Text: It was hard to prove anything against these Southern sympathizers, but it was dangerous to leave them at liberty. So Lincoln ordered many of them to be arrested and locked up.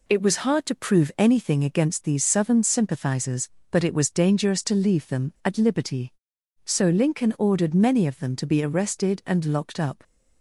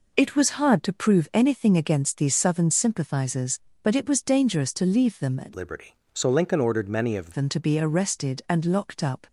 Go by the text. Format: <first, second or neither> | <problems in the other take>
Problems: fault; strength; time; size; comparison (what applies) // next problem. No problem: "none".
first | changes voice from "liberty" to "of"; from 5.5 to 7.3 s; 1.8 s long